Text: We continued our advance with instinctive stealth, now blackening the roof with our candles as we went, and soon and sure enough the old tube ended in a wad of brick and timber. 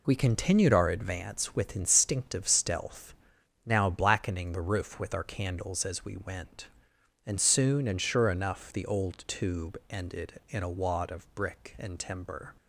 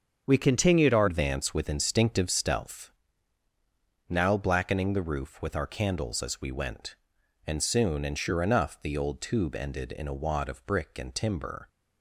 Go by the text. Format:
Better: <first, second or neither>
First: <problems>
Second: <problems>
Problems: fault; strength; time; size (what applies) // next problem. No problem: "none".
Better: first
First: none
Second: starts louder than the rest; until 1.2 s; 7 dB // changes voice at "advance"; from 1.0 s on; 10.6 s long